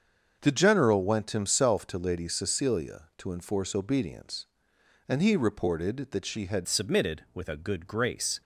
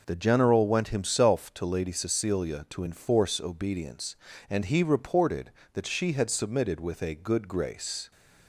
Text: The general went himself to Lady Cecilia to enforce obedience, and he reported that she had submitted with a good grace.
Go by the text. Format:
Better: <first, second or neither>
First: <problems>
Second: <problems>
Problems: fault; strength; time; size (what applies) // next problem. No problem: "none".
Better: second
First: starts louder than the rest; until 1.4 s; 6.5 dB // changes voice at "submitted"; from 6.6 s on; 1.8 s long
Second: none